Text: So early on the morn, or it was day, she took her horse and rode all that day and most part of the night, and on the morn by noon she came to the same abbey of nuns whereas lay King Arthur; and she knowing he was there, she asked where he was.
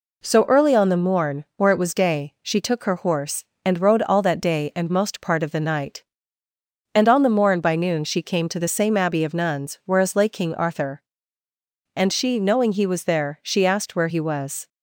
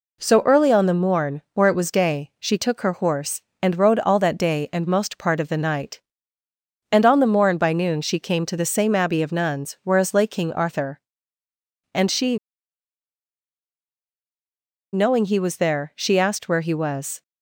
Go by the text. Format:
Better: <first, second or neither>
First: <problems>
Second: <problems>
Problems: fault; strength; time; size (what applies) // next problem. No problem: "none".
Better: first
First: none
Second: pauses between "she" and "knowing"; strong; at 12.3 s; 2.5 s long